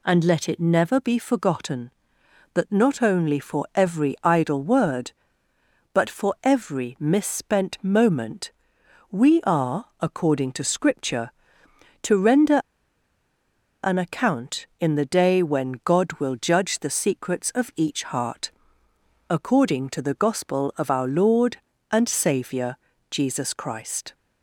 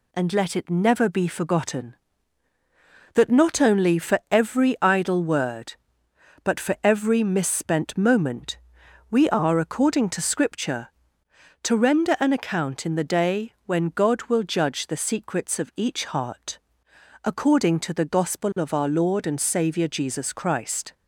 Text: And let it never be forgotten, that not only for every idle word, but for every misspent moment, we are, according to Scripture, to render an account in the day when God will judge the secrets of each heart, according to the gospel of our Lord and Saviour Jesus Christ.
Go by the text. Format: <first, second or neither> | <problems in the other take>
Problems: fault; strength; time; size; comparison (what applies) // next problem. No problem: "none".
second | pauses between "render" and "an"; strong; at 12.5 s; 1.2 s long // pauses between "Saviour" and "Jesus"; slight; at 22.7 s; 0.34 s long